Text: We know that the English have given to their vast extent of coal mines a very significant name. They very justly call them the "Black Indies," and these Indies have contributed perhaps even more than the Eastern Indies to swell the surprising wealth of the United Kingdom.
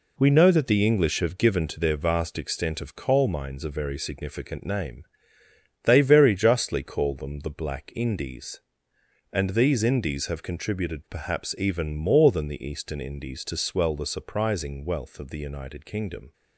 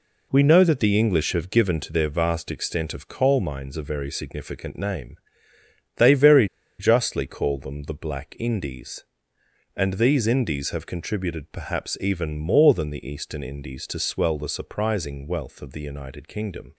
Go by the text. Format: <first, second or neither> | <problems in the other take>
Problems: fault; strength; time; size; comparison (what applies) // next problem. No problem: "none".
first | pauses between "very" and "justly"; slight; at 6.4 s; 0.33 s long